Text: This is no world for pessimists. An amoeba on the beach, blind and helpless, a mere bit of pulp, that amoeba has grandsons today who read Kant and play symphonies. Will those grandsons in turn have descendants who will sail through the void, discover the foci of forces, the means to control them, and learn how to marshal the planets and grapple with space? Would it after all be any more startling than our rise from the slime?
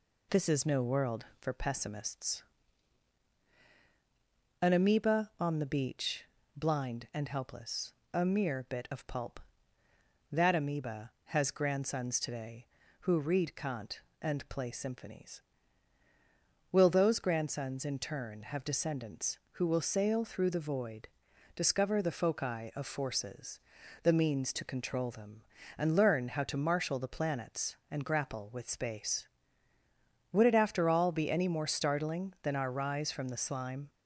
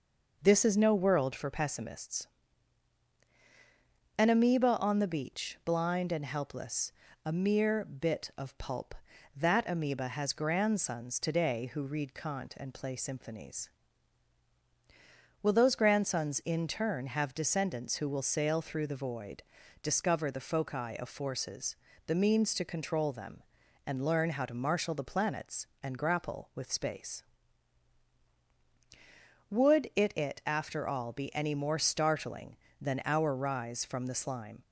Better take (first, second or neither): first